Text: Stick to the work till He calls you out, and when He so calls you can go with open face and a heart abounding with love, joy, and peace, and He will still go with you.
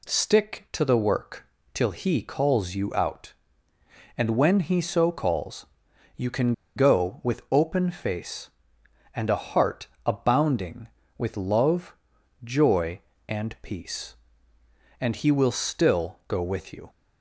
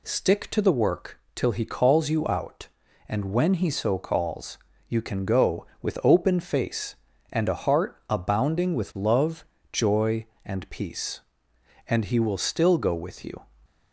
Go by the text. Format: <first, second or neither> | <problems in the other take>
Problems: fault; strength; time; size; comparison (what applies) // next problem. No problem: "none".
second | pauses between "work" and "till"; slight; at 1.4 s; 0.26 s long; slight in the second // pauses between "calls" and "you"; noticeable; at 5.6 s; 0.50 s long; slight in the second // pauses between "can" and "go"; slight; at 6.5 s; 0.23 s long // pauses between "heart" and "abounding"; slight; at 9.8 s; 0.18 s long